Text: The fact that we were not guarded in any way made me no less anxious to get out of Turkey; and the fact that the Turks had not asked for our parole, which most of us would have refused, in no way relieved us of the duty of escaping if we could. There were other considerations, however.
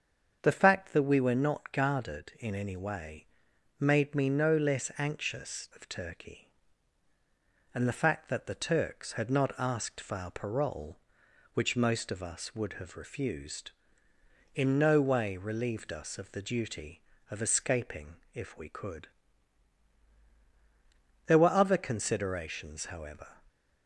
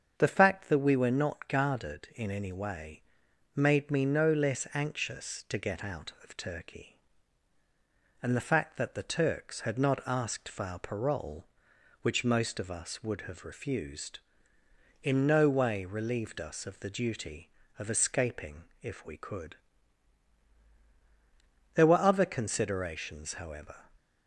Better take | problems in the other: second | starts louder than the rest; strong; until 1.4 s; 7 dB; also in the second // pauses between "way" and "made"; noticeable; at 3.2 s; 0.52 s long; noticeable in the second // skips "to get out"; at 5.7 s // pauses between "escaping" and "if"; slight; at 18.1 s; 0.16 s long; slight in the second

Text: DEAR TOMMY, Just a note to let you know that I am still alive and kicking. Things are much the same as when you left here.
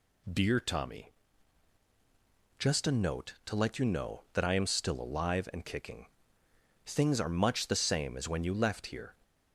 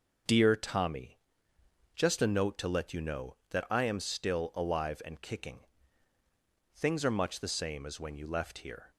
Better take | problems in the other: neither | none

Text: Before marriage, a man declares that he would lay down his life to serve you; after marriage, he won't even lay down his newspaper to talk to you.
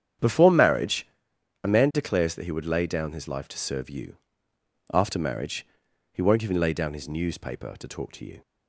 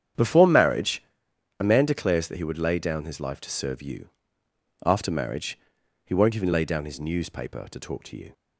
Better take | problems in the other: neither | starts louder than the rest; strong; the same in both

